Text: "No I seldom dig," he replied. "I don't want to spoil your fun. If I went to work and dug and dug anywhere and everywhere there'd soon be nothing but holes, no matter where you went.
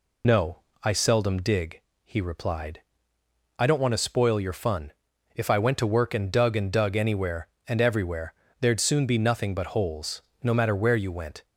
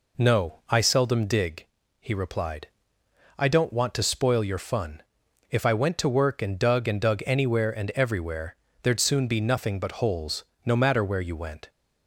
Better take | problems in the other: second | loses the start of "No"; at 0.2 s; 45 ms // pauses between "No" and "I"; slight; at 0.5 s; 0.24 s long // pauses between "everywhere" and "there'd"; slight; at 8.3 s; 0.26 s long; slight in the second

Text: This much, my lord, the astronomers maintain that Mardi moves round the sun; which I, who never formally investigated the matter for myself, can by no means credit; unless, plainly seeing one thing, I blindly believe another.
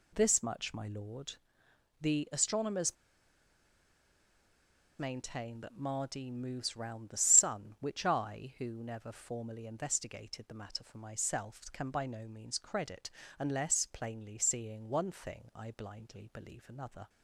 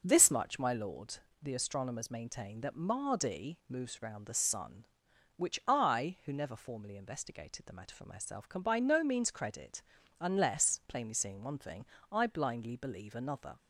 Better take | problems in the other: second | pauses between "astronomers" and "maintain"; strong; at 2.9 s; 2.0 s long

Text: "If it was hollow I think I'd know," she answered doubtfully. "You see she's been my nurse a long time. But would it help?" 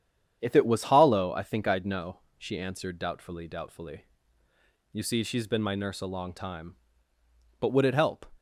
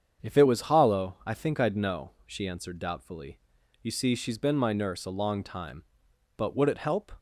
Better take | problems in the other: second | starts louder than the rest; strong; until 1.4 s; 9 dB; strong in the second // says "doubtfully" twice; at 3.4 s

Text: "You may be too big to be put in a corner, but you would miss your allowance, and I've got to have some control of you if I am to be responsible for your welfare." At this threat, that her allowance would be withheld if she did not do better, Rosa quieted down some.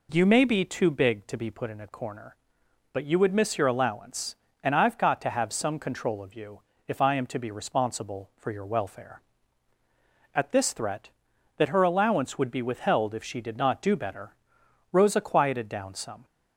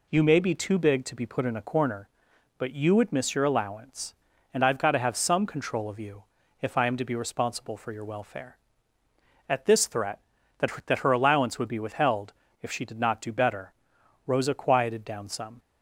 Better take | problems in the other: first | pauses between "you" and "if"; at 6.2 s; 0.38 s long; slight in the first // says "that" twice; at 10.8 s // pauses between "withheld" and "if"; slight; at 12.3 s; 0.28 s long

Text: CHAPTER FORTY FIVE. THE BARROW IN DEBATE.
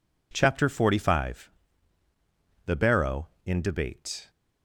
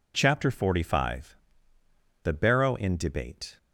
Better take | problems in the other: neither | none

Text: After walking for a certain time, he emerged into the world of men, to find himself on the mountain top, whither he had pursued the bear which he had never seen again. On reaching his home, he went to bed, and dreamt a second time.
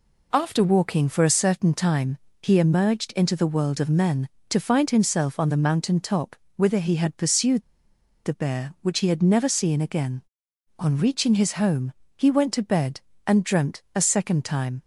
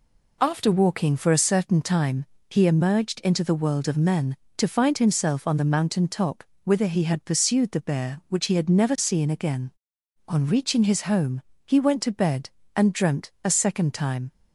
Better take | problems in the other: second | pauses between "pursued" and "the"; noticeable; at 7.6 s; 0.63 s long

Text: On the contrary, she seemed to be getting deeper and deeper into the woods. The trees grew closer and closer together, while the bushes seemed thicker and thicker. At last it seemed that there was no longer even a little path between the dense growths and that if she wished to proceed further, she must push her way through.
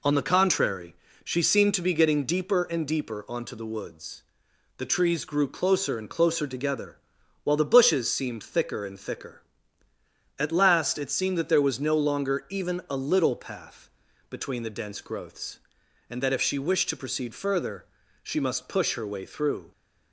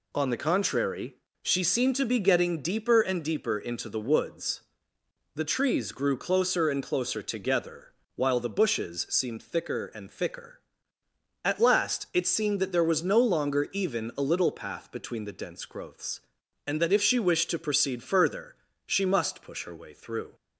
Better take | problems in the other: second | says "onto" for "into"; at 3.2 s // pauses between "path" and "between"; at 13.8 s; 0.40 s long

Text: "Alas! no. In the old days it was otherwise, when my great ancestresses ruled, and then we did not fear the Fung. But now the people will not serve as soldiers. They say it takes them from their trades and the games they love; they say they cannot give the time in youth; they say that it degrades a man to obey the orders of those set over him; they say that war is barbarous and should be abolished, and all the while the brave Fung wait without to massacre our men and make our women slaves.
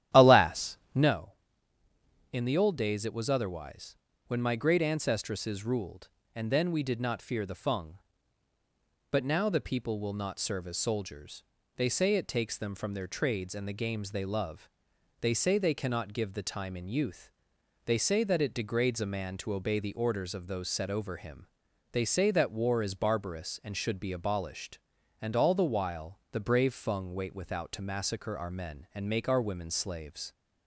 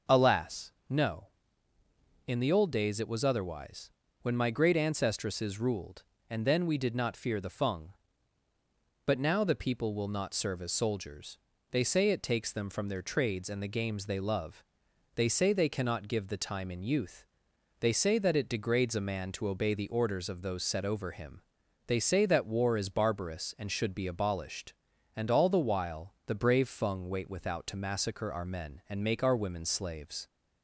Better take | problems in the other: second | starts louder than the rest; strong; until 1.2 s; 11.5 dB

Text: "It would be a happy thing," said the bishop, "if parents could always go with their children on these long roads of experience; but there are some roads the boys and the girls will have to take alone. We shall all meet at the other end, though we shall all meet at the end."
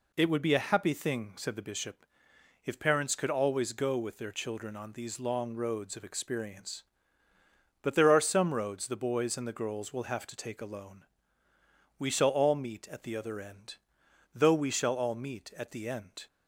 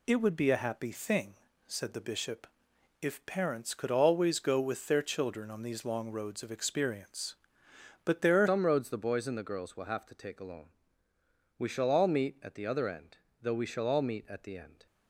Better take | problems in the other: first | changes voice at "some"; from 8.4 s on; 6.4 s long

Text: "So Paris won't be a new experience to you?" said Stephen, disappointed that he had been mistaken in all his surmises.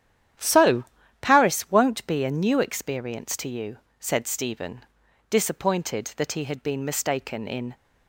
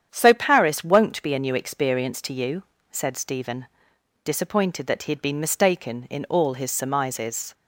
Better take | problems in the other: second | starts louder than the rest; strong; until 1.7 s; 10 dB; strong in the second // pauses between "So" and "Paris"; slight; at 0.8 s; 0.36 s long // stops before "all his surmises"; at 7.7 s

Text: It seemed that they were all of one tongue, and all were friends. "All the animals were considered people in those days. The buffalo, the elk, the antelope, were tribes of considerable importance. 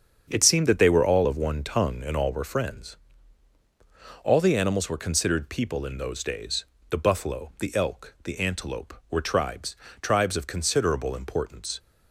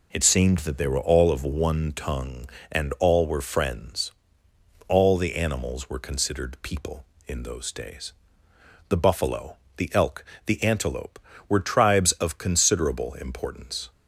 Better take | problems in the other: second | starts louder than the rest; strong; until 1.3 s; 7 dB // says "tribes" twice; at 10.0 s

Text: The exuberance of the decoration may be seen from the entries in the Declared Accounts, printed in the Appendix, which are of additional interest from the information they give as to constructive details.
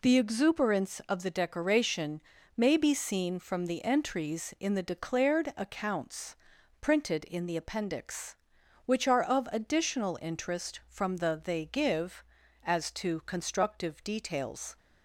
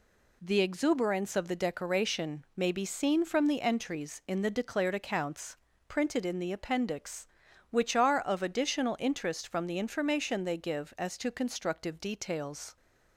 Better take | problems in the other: second | pauses between "decoration" and "may"; slight; at 2.2 s; 0.34 s long // skips "information"; at 11.4 s

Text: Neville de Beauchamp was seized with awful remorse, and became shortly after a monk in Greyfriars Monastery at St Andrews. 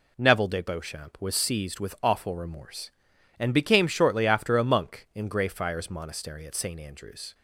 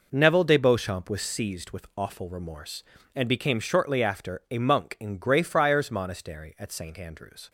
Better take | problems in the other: neither | none

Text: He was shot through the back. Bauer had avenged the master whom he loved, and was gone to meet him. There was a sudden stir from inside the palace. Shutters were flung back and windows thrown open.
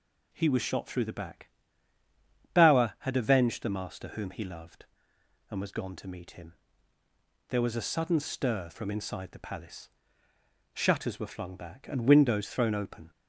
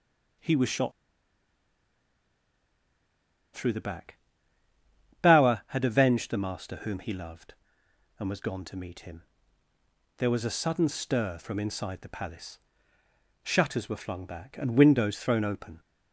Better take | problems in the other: first | pauses between "shot" and "through"; strong; at 0.9 s; 2.6 s long

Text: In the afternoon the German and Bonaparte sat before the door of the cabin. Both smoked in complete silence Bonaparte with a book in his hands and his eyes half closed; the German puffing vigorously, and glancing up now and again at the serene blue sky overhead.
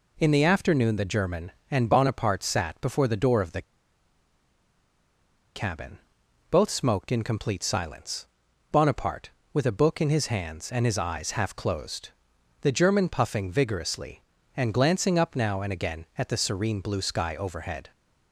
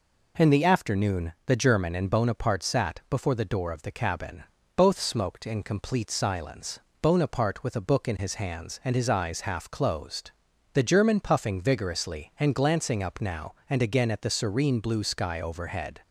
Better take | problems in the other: second | pauses between "the" and "cabin"; strong; at 3.6 s; 1.9 s long // pauses between "silence" and "Bonaparte"; noticeable; at 8.2 s; 0.46 s long; slight in the second

